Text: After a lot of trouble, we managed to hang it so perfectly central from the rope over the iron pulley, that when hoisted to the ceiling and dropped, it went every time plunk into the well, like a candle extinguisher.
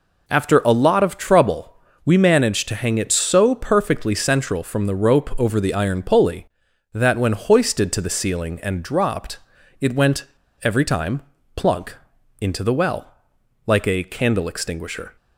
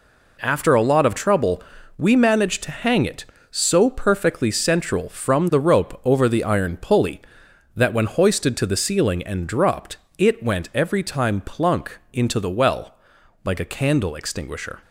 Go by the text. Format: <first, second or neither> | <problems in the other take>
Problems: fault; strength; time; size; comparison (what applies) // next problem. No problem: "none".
second | pauses between "went" and "every"; at 10.2 s; 0.37 s long // pauses between "time" and "plunk"; slight; at 11.2 s; 0.34 s long // pauses between "plunk" and "into"; at 11.9 s; 0.44 s long